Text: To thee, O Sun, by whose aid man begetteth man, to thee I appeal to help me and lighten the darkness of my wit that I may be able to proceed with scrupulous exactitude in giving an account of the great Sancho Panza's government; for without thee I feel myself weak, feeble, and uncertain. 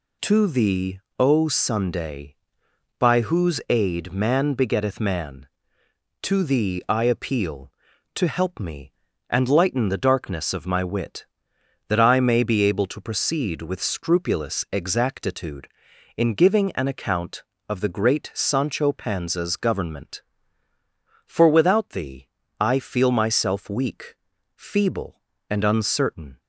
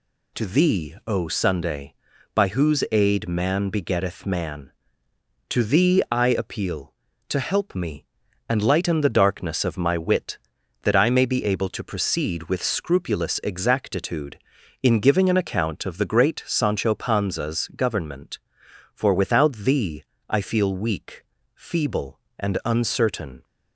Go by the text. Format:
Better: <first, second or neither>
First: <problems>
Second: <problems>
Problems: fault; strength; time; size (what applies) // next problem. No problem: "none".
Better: first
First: pauses between "thee" and "I"; slight; at 22.2 s; 0.32 s long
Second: pauses between "thee" and "I"; slight; at 20.0 s; 0.24 s long // skips "myself"; at 20.7 s